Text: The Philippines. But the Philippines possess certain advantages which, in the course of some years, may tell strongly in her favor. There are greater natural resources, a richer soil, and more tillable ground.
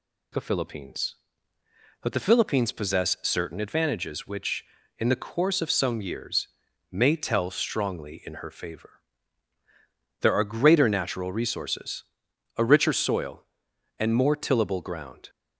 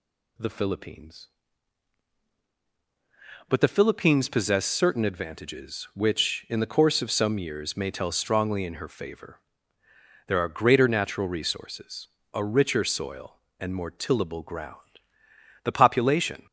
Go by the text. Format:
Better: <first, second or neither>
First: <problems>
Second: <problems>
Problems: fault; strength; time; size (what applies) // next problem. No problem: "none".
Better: first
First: none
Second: goes on to say "The population"; noticeable; from 15.6 s on; 0.82 s long